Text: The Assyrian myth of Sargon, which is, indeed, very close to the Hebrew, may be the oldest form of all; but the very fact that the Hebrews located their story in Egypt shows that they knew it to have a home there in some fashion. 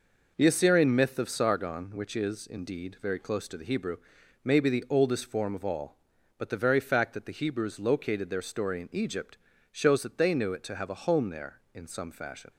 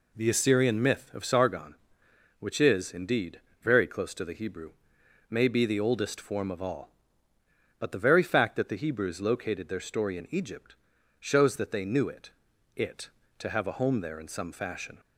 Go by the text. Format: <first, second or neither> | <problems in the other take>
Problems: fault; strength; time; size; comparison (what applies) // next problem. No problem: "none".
first | pauses between "Egypt" and "shows"; at 10.7 s; 0.42 s long; slight in the first // says "it" twice; at 12.7 s